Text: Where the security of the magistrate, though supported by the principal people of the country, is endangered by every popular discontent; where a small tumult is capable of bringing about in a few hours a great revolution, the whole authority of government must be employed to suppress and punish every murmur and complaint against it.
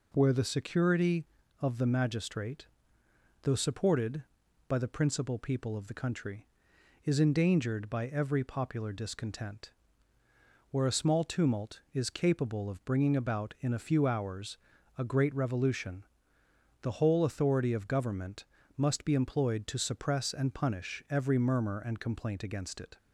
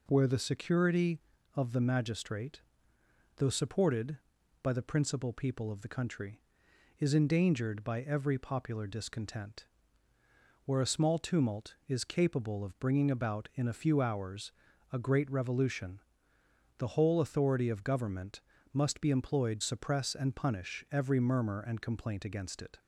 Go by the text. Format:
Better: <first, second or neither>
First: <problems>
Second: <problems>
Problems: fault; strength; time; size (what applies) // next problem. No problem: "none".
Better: first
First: pauses between "hours" and "a"; at 14.5 s; 0.40 s long // pauses between "government" and "must"; slight; at 18.4 s; 0.32 s long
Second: pauses between "hours" and "a"; at 14.5 s; 0.40 s long // pauses between "government" and "must"; slight; at 18.3 s; 0.32 s long // skips "to"; at 19.6 s